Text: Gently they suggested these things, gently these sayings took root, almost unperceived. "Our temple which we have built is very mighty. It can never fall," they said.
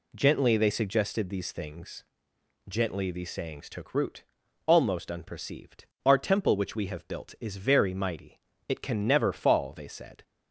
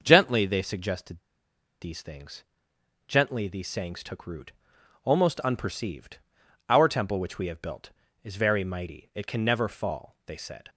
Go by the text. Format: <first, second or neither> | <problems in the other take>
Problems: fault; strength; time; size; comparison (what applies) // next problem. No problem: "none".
first | starts louder than the rest; until 1.0 s; 6.5 dB // pauses between "suggested" and "these"; noticeable; at 1.1 s; 0.62 s long